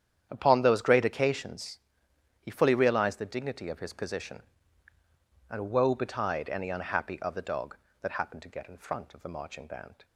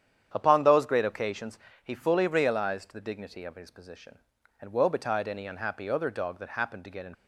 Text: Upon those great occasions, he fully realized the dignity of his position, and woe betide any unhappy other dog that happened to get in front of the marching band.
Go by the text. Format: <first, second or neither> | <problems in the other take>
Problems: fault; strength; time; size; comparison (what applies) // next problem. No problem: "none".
first | starts louder than the rest; strong; until 1.3 s; 9 dB; strong in the first // stops before "front of the marching band"; at 7.1 s